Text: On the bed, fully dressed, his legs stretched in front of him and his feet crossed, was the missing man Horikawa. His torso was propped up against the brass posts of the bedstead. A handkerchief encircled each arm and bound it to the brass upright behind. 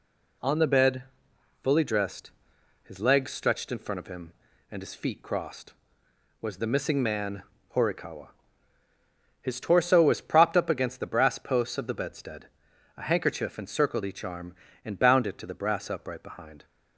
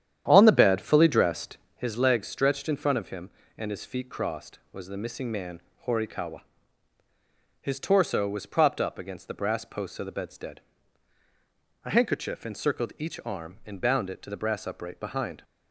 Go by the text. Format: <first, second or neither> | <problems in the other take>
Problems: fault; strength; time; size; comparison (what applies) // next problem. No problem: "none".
first | starts louder than the rest; strong; until 1.8 s; 10 dB // pauses between "man" and "Horikawa"; slight; at 5.6 s; 0.26 s long; slight in the first